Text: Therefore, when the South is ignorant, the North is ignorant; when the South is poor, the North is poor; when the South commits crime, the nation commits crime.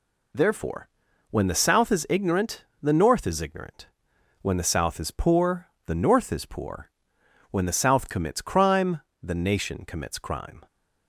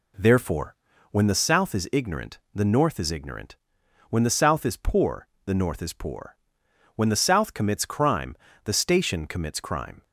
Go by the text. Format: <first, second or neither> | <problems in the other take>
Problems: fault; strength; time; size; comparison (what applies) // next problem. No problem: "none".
first | says "station" for "nation"; at 8.7 s